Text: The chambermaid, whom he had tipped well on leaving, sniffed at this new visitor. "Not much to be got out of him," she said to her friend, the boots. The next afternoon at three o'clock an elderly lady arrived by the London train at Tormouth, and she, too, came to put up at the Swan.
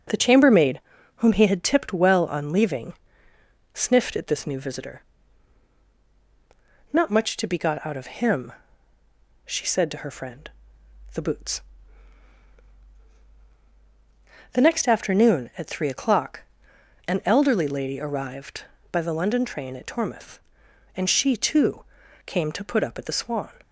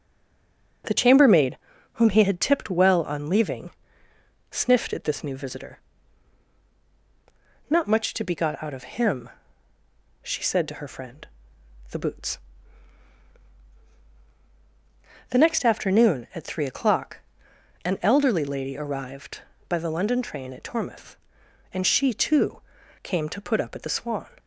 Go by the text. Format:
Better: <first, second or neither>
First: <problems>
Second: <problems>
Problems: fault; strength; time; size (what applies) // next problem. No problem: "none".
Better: first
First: starts louder than the rest; noticeable; until 1.4 s; 6 dB // pauses between "o'clock" and "an"; noticeable; at 16.4 s; 0.66 s long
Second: stays silent before the first word; slight; until 0.8 s; 0.8 s long // starts louder than the rest; noticeable; until 2.2 s; 6 dB // pauses between "o'clock" and "an"; noticeable; at 17.1 s; 0.66 s long